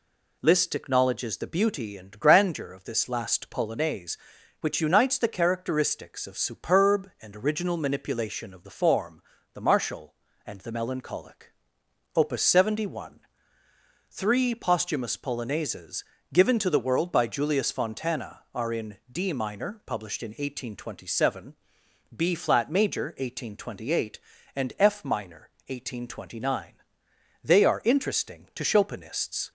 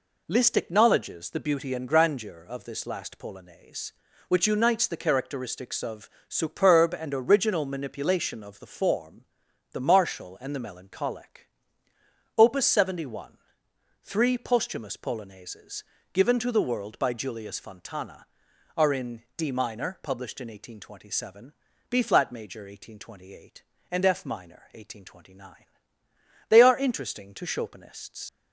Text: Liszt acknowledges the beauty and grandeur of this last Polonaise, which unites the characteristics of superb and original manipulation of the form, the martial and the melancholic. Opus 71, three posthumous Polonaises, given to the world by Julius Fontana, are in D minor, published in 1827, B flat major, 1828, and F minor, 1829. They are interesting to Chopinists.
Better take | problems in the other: first | pauses between "of" and "superb"; slight; at 6.0 s; 0.22 s long // pauses between "in" and "D"; slight; at 19.2 s; 0.16 s long; slight in the first // leaves "Chopinists" unfinished; at 28.2 s; 95 ms

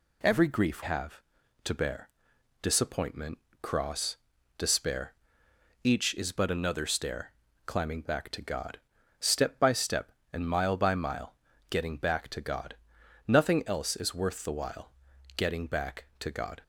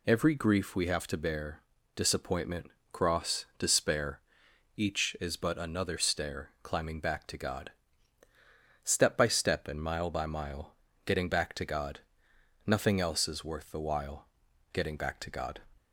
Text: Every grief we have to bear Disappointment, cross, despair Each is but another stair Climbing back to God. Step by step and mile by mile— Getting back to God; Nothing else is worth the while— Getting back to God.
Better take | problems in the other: second | skips "we"; at 0.8 s // pauses between "bear" and "Disappointment"; noticeable; at 2.0 s; 0.52 s long; slight in the second // pauses between "despair" and "Each"; noticeable; at 5.1 s; 0.70 s long; noticeable in the second // pauses between "stair" and "Climbing"; slight; at 7.3 s; 0.34 s long

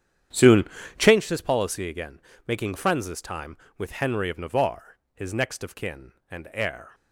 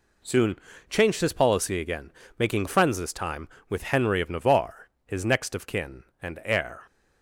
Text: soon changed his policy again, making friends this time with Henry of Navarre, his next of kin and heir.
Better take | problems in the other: second | starts louder than the rest; strong; until 1.2 s; 9.5 dB // pauses between "soon" and "changed"; slight; at 0.6 s; 0.34 s long; slight in the second

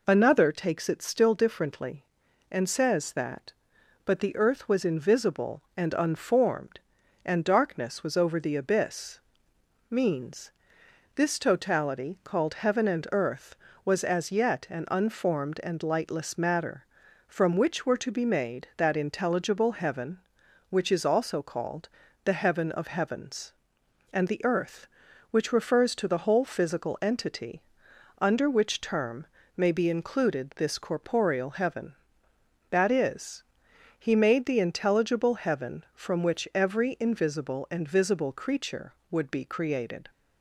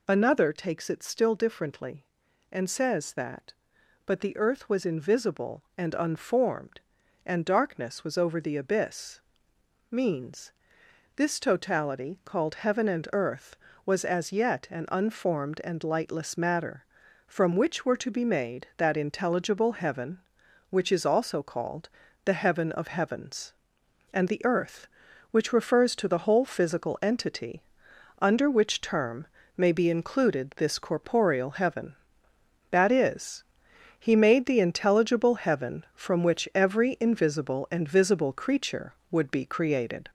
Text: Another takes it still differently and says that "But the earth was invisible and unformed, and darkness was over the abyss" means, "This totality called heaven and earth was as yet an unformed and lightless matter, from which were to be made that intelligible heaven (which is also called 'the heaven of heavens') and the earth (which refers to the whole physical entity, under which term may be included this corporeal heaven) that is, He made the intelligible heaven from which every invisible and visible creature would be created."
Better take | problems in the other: first | gets louder; noticeable; throughout; 5 dB // pauses between "abyss" and "means"; noticeable; at 9.1 s; 0.70 s long; noticeable in the first // pauses between "called" and "the"; at 21.8 s; 0.38 s long; also in the first // pauses between "term" and "may"; slight; at 29.2 s; 0.30 s long; slight in the first

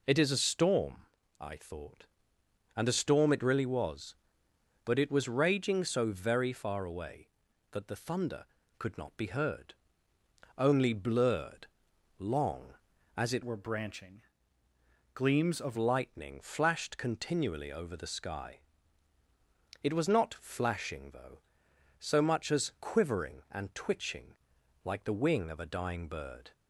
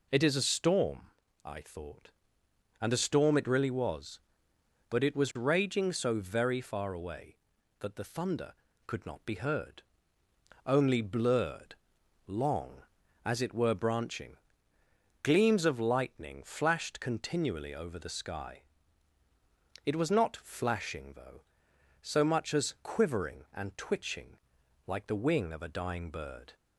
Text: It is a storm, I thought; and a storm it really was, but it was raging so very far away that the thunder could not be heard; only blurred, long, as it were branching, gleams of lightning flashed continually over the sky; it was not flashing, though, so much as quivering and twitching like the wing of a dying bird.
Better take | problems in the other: second | changes voice from "were" to "of"; from 13.4 to 15.7 s; 2.3 s long // pauses between "twitching" and "like"; noticeable; at 24.3 s; 0.50 s long; noticeable in the second

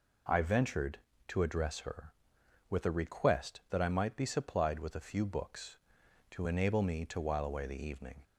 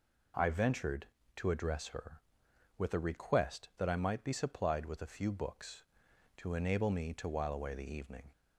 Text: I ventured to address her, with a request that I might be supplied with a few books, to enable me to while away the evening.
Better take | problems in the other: neither | none

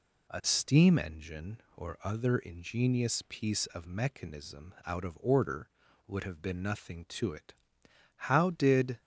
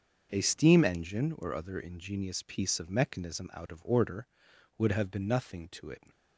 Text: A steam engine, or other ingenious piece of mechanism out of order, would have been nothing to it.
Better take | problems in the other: second | goes on to say "How did"; noticeable; from 8.1 s on; 0.84 s long

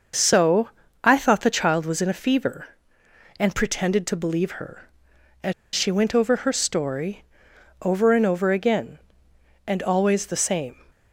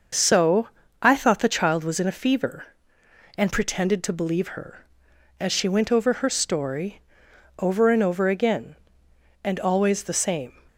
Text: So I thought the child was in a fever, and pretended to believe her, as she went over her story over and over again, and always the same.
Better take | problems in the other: second | starts louder than the rest; until 1.4 s; 6.5 dB; also in the second // pauses between "So" and "I"; slight; at 0.6 s; 0.34 s long; slight in the second // pauses between "as" and "she"; slight; at 5.5 s; 0.22 s long // pauses between "story" and "over"; noticeable; at 7.2 s; 0.60 s long; noticeable in the second

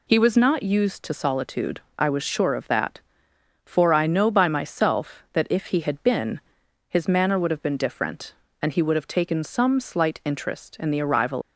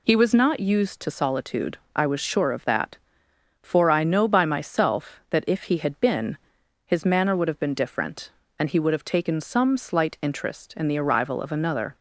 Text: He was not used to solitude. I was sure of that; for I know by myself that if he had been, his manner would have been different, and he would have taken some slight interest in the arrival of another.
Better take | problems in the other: second | stops before "of another"; at 11.4 s

